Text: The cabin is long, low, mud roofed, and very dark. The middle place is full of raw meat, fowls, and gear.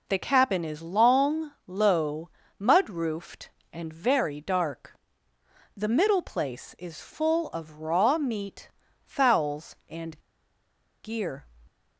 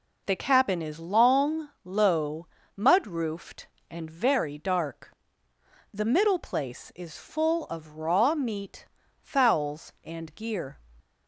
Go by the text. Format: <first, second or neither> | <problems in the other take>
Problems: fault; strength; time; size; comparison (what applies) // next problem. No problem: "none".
second | pauses between "and" and "gear"; noticeable; at 10.1 s; 0.87 s long